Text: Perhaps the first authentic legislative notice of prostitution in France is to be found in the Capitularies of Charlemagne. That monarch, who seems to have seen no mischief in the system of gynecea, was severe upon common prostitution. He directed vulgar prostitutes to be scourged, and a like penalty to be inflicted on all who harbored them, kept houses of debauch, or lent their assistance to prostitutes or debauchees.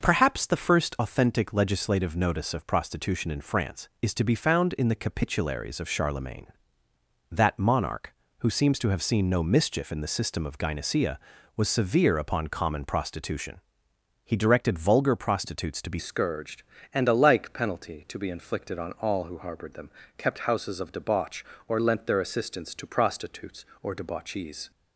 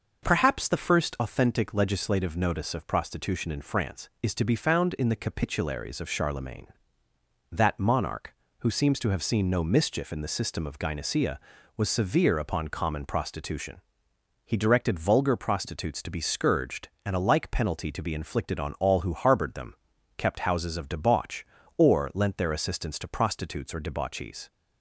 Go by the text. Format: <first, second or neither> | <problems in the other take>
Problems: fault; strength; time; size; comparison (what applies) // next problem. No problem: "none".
second | starts louder than the rest; noticeable; until 1.0 s; 6 dB; noticeable in the second // changes voice at "scourged"; from 15.9 s on; 8.8 s long